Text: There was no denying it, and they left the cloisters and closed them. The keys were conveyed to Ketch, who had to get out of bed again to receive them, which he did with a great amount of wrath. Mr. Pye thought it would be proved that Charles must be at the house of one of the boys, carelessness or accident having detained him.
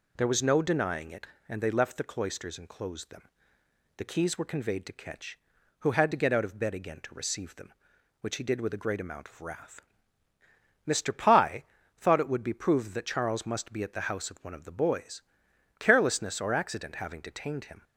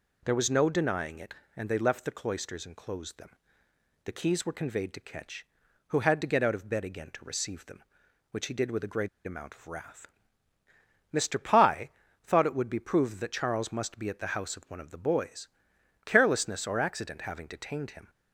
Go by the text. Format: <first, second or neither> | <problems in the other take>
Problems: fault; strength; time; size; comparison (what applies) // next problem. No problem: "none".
first | pauses between "great" and "amount"; slight; at 9.0 s; 0.16 s long // pauses between "Pye" and "thought"; slight; at 11.8 s; 0.36 s long; slight in the first